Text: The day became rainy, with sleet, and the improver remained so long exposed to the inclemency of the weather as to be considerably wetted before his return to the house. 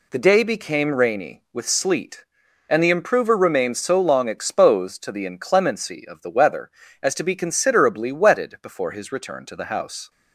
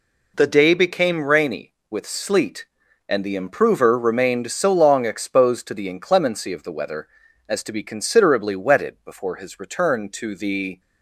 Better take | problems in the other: first | stops before "house"; at 10.7 s

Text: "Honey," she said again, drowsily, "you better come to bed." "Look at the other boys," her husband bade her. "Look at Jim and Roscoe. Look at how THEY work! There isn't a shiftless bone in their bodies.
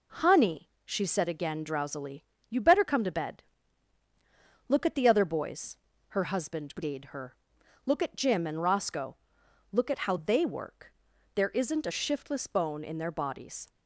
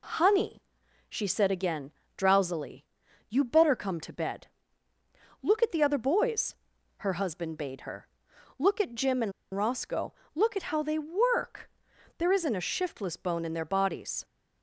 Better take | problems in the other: first | pauses between "and" and "Roscoe"; slight; at 9.3 s; 0.22 s long

